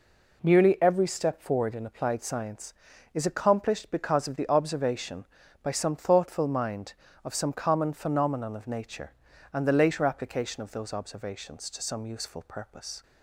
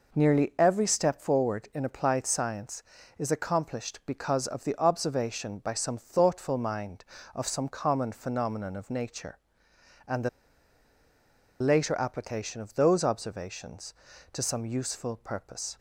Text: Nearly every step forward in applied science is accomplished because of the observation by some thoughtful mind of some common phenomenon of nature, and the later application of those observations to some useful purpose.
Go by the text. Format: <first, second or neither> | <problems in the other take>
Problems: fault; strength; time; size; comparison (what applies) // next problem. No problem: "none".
first | pauses between "the" and "later"; strong; at 10.2 s; 1.3 s long